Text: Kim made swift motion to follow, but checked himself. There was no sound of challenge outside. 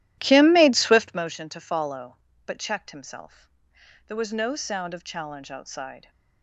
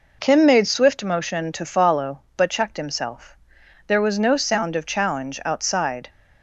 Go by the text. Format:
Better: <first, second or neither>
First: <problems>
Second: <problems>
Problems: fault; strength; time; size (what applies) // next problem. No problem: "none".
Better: second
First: starts louder than the rest; strong; until 1.2 s; 13.5 dB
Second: none